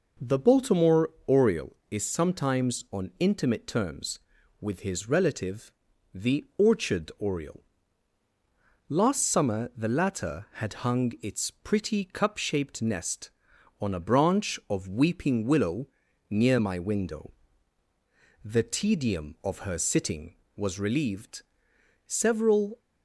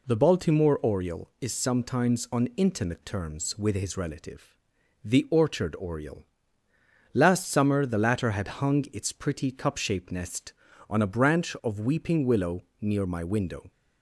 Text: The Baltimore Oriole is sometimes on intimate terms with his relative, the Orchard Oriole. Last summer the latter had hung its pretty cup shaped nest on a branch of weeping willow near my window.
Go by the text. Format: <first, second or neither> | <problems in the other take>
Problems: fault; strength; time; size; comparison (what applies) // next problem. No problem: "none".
second | pauses between "Baltimore" and "Oriole"; slight; at 1.0 s; 0.18 s long // pauses between "willow" and "near"; at 15.8 s; 0.42 s long; slight in the second // goes on to say "The tedium of her sitting was relieved several"; strong; from 18.4 s on; 4.3 s long